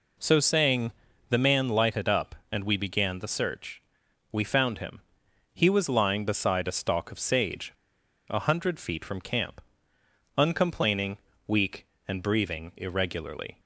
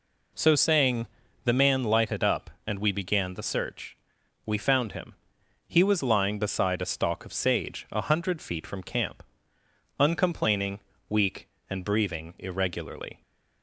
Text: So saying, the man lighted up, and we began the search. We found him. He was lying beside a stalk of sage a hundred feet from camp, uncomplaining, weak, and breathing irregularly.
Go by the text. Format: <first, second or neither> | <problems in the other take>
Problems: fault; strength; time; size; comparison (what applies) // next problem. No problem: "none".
second | pauses between "sage" and "a"; noticeable; at 7.7 s; 0.57 s long